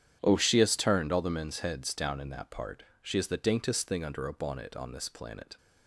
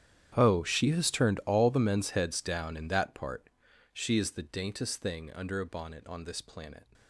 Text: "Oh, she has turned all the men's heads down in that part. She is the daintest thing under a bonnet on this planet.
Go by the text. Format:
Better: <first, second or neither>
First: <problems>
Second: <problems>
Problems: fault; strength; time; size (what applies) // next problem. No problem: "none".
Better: first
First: starts louder than the rest; strong; until 1.2 s; 9.5 dB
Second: gets quieter; strong; throughout; 20 dB // starts louder than the rest; strong; until 1.3 s; 10 dB